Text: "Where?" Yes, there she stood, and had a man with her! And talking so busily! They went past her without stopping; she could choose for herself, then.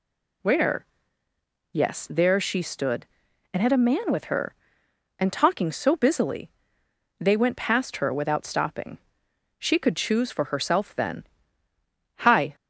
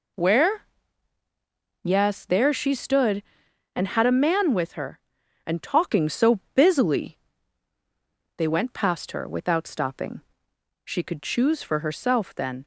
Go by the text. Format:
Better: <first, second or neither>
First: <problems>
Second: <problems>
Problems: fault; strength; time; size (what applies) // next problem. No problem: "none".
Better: second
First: goes on to say "Hi"; slight; from 12.2 s on; 0.34 s long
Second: none